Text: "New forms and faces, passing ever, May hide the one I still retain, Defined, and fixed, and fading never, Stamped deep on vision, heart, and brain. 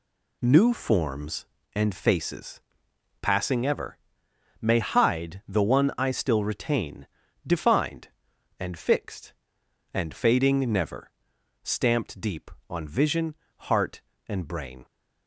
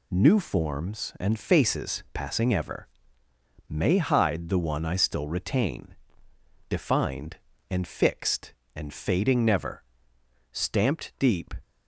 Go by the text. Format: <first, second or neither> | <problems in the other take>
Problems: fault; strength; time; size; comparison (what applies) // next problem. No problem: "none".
first | stops before "on vision heart and brain"; at 11.6 s